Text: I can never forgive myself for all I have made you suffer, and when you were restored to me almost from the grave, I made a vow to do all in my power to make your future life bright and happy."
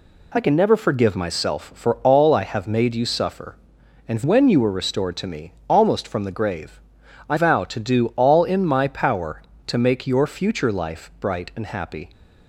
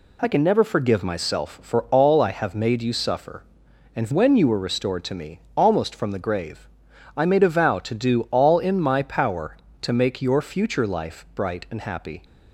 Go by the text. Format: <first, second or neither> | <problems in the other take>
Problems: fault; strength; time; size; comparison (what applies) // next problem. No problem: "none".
second | pauses between "me" and "almost"; slight; at 5.5 s; 0.16 s long; slight in the second // skips "made a"; at 7.3 s